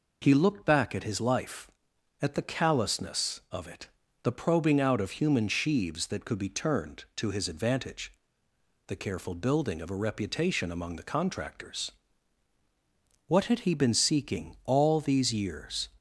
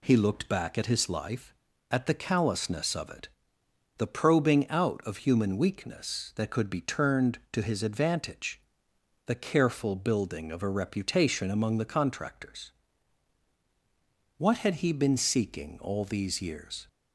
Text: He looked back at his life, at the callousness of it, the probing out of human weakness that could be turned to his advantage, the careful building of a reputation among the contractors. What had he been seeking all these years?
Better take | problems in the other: second | says "sheaves" for "weakness"; at 5.4 s

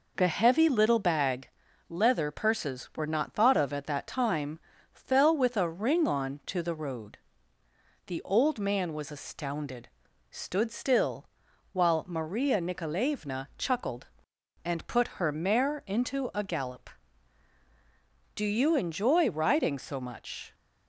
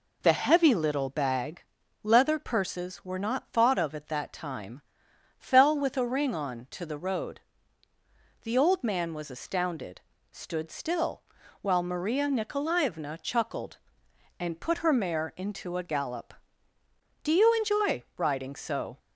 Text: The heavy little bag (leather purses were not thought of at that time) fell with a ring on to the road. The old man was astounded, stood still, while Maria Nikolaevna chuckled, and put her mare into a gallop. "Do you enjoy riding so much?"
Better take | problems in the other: first | stops before "much"; at 18.9 s

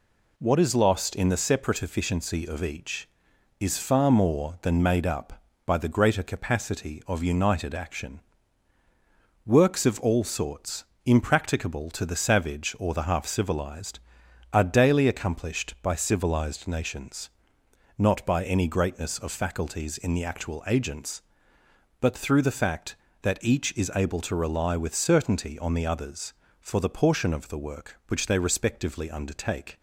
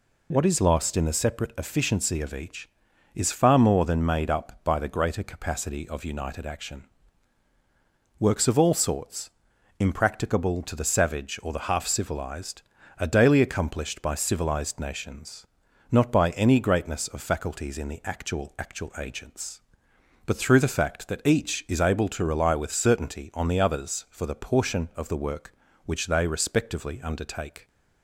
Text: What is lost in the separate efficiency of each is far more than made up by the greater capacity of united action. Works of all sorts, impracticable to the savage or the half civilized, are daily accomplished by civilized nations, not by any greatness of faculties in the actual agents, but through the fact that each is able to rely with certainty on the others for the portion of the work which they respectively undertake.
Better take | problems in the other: first | says "actual" twice; at 18.5 s

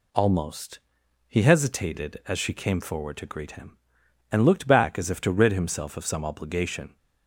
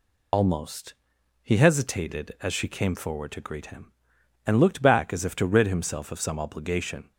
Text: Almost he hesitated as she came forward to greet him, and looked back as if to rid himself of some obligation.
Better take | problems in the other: first | loses the start of "Almost"; at 0.3 s; 65 ms // pauses between "Almost" and "he"; noticeable; at 0.9 s; 0.48 s long; noticeable in the first

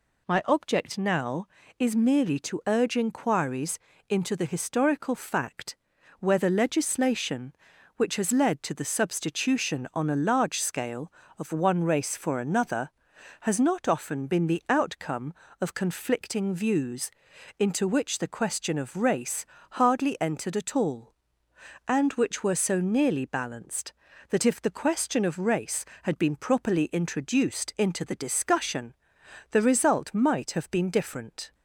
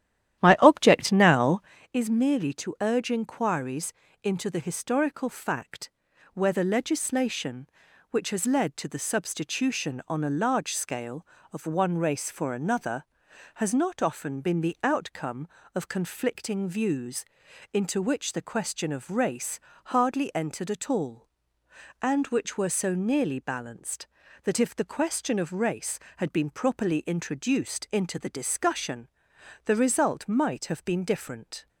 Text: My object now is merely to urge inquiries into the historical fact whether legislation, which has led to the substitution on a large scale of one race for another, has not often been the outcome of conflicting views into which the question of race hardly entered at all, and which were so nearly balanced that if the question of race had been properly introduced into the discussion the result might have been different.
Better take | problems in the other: first | starts louder than the rest; strong; until 1.9 s; 12 dB // pauses between "inquiries" and "into"; slight; at 3.9 s; 0.30 s long; slight in the first // pauses between "fact" and "whether"; at 5.8 s; 0.44 s long; also in the first // pauses between "views" and "into"; noticeable; at 17.2 s; 0.50 s long; noticeable in the first // pauses between "race" and "hardly"; slight; at 19.5 s; 0.28 s long; slight in the first // pauses between "discussion" and "the"; noticeable; at 29.0 s; 0.58 s long; noticeable in the first

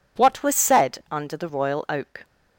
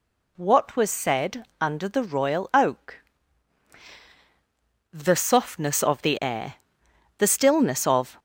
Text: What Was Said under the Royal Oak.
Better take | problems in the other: first | pauses between "Said" and "under"; slight; at 1.4 s; 0.16 s long // goes on to say "The softness of the air the stillness of"; strong; from 4.9 s on; 3.2 s long

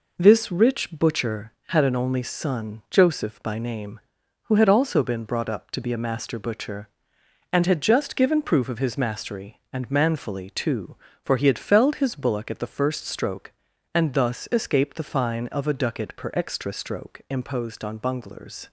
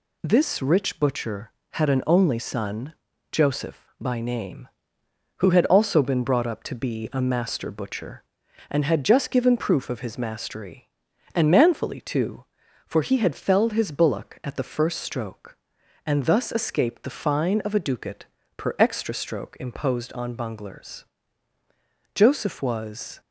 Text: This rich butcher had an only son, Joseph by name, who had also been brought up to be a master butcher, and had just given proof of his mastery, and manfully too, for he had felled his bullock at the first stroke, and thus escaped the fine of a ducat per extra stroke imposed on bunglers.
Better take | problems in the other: first | pauses between "ducat" and "per"; slight; at 18.2 s; 0.32 s long // goes on to say "Joseph was"; noticeable; from 22.1 s on; 1.0 s long

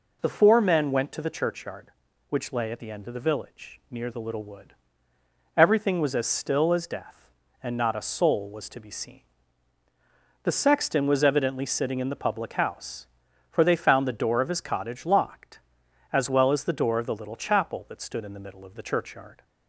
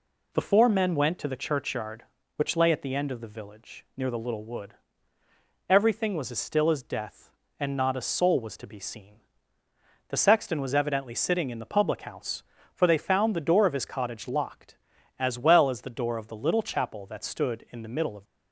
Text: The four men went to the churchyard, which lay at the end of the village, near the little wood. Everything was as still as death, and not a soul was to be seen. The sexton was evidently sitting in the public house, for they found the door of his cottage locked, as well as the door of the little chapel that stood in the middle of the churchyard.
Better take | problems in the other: first | stops before "the churchyard"; at 18.2 s

